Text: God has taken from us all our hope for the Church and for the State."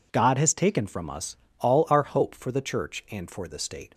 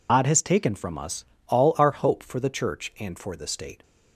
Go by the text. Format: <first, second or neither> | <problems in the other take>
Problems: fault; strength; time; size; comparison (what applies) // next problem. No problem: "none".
first | loses the start of "God"; at 0.0 s; 100 ms // pauses between "us" and "all"; slight; at 1.2 s; 0.24 s long; slight in the first